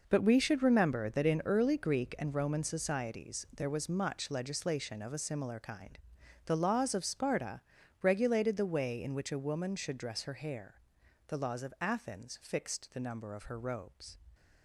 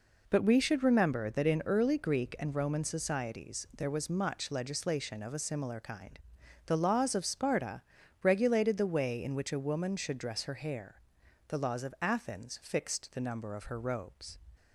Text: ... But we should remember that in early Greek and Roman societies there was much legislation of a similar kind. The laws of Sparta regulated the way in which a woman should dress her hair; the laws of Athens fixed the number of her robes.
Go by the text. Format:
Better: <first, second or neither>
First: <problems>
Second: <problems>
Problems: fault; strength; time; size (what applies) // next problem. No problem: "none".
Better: second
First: gets quieter; strong; throughout; 12 dB // pauses between "Sparta" and "regulated"; at 7.6 s; 0.42 s long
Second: pauses between "Sparta" and "regulated"; at 7.8 s; 0.42 s long